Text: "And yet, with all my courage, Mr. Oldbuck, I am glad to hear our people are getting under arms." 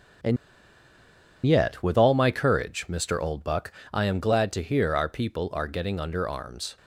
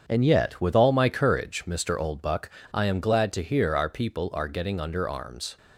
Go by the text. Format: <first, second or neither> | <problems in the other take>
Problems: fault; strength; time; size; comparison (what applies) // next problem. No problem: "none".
second | starts louder than the rest; strong; until 2.3 s; 7 dB; strong in the second // pauses between "And" and "yet"; at 0.3 s; 1.1 s long